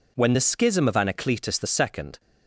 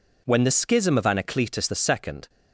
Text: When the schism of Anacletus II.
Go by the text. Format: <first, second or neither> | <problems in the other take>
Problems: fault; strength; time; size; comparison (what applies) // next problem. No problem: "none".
neither | none